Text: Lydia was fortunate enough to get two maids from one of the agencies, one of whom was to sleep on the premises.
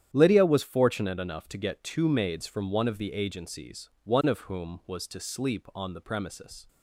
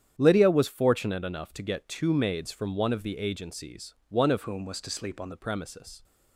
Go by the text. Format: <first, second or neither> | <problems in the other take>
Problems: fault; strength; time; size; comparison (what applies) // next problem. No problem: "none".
first | starts louder than the rest; strong; until 1.2 s; 9 dB; strong in the first // changes voice from "whom" to "on"; from 4.4 to 5.3 s; 0.9 s long